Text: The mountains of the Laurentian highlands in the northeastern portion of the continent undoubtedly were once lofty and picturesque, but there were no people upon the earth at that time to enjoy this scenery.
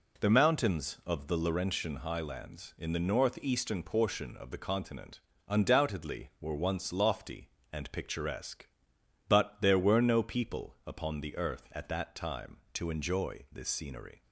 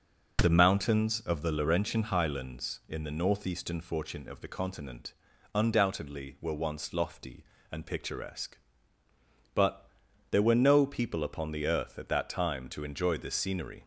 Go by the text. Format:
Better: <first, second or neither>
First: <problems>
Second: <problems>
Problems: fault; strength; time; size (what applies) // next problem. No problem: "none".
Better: first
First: pauses between "continent" and "undoubtedly"; slight; at 5.2 s; 0.26 s long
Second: says "fortune" for "portion"; at 3.8 s // pauses between "continent" and "undoubtedly"; at 5.1 s; 0.42 s long // pauses between "but" and "there"; at 9.8 s; 0.44 s long